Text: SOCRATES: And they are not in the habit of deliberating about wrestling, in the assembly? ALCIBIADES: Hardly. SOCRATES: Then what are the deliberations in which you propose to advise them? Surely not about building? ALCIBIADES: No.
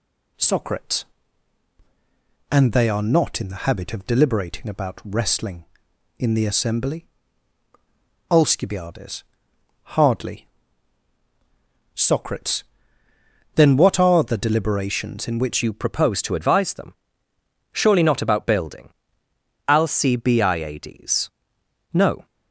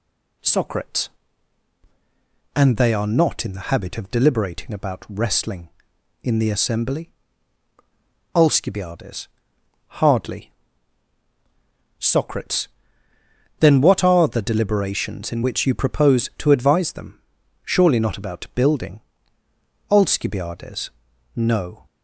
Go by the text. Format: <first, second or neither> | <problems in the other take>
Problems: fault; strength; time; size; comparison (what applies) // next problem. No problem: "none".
second | changes voice at "you"; from 15.6 s on; 6.6 s long